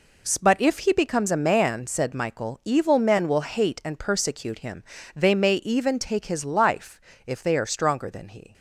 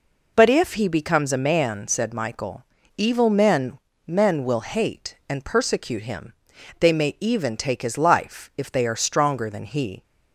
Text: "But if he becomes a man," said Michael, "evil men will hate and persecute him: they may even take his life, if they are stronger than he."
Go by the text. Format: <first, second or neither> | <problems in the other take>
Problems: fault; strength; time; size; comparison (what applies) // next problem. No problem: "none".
first | says "men" twice; at 4.0 s